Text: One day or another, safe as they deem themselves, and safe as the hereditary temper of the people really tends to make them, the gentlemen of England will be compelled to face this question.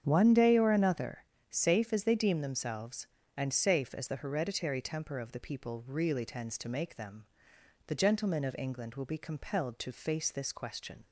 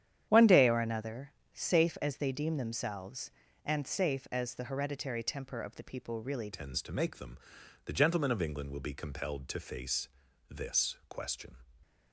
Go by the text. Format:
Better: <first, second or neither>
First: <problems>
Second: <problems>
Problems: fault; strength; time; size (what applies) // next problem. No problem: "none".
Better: first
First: starts louder than the rest; strong; until 1.0 s; 8 dB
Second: starts louder than the rest; strong; until 1.2 s; 9.5 dB // changes voice at "tends"; from 6.5 s on; 5.0 s long // pauses between "face" and "this"; at 10.0 s; 0.42 s long